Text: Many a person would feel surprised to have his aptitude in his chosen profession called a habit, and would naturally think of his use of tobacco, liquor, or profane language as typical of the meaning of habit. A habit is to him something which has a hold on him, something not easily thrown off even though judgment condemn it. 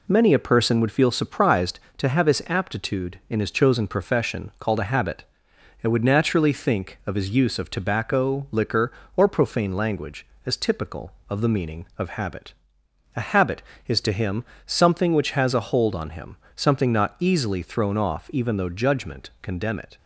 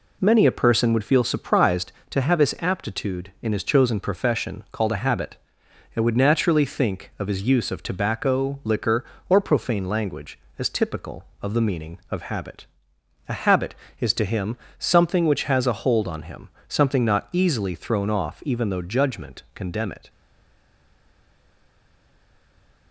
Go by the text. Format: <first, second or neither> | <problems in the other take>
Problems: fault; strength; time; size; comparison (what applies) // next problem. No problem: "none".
first | pauses between "him" and "something"; slight; at 14.5 s; 0.20 s long; slight in the first // stays silent after the last word; strong; from 20.0 s on; 2.9 s long